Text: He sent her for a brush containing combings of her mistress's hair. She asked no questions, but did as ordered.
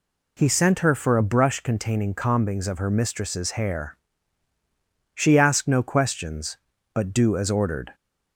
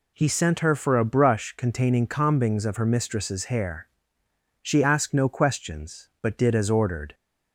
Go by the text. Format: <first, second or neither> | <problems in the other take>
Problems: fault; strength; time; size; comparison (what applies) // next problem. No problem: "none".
second | says "do" for "did"; at 7.1 s